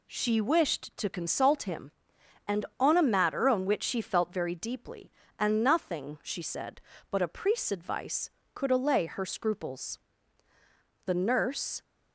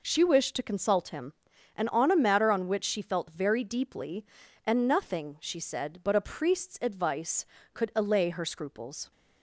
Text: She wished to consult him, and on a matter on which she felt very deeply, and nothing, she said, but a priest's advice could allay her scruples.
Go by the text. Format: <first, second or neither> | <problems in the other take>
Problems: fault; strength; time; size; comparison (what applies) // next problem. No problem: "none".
second | goes on to say "The nurse"; noticeable; from 11.0 s on; 0.78 s long